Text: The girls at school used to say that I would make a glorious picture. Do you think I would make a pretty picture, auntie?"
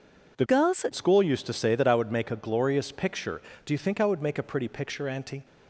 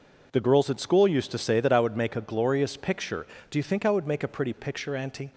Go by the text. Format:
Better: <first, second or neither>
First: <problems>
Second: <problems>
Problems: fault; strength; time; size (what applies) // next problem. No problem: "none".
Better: second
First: changes voice from "girls" to "at"; from 0.4 to 0.9 s; 0.5 s long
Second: none